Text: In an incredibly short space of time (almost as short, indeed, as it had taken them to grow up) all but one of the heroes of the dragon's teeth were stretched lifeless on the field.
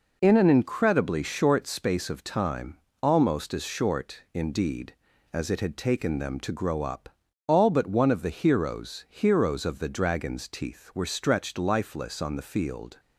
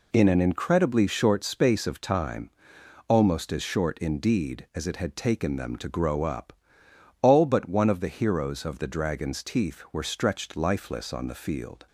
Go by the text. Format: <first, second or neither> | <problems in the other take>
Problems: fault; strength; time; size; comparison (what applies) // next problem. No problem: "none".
second | says "heroes" twice; at 9.0 s